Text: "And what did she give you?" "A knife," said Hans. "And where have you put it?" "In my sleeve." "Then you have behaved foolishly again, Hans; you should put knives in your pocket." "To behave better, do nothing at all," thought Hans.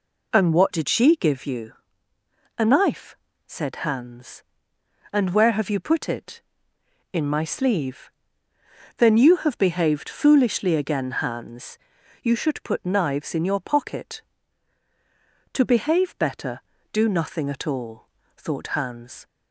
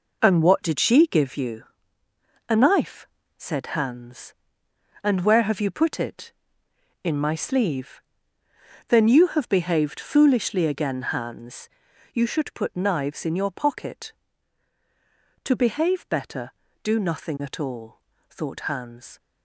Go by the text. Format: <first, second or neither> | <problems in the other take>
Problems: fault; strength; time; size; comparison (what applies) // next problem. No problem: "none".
first | gets quieter; throughout; 7 dB